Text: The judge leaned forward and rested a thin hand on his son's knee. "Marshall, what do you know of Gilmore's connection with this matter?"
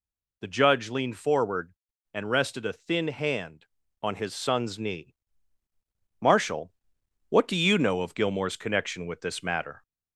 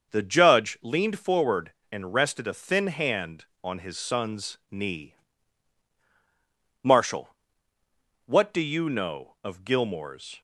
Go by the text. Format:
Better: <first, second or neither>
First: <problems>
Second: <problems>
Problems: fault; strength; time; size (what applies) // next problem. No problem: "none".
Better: first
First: none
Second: starts louder than the rest; until 1.1 s; 6.5 dB // stops before "connection with this matter"; at 10.3 s